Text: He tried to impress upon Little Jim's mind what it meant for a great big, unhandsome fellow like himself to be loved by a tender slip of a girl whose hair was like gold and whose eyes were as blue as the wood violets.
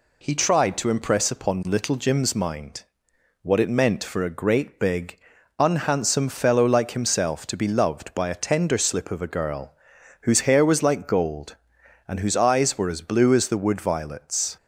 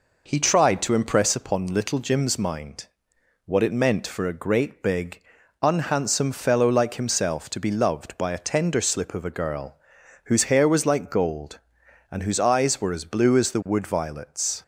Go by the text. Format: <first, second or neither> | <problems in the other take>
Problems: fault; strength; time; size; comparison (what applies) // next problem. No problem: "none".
first | starts louder than the rest; noticeable; until 1.5 s; 4.5 dB // pauses between "mind" and "what"; noticeable; at 2.8 s; 0.58 s long; noticeable in the first // pauses between "girl" and "whose"; noticeable; at 9.7 s; 0.48 s long; noticeable in the first